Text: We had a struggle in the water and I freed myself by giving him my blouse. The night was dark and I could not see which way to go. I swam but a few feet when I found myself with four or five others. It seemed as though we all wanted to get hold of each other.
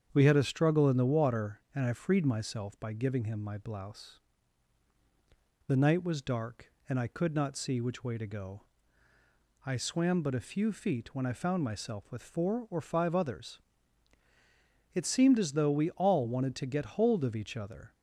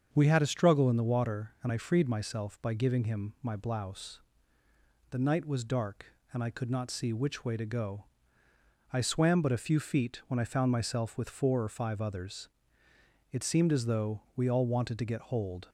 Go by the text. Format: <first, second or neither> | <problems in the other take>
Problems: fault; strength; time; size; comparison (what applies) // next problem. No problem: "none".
first | starts louder than the rest; until 1.1 s; 7 dB; strong in the first // pauses between "though" and "we"; slight; at 14.1 s; 0.16 s long // stops before "of each other"; at 15.6 s